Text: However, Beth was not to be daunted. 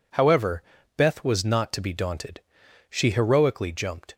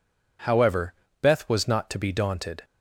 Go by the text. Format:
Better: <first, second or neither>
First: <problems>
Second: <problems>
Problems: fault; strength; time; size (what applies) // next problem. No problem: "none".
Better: second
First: goes on to say "She heroically jumped"; noticeable; from 2.9 s on; 1.2 s long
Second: none